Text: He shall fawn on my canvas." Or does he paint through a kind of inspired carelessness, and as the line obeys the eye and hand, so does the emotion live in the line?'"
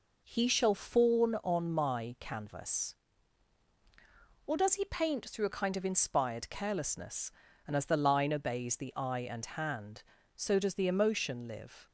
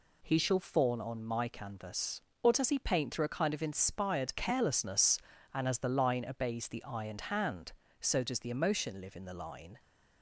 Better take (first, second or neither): second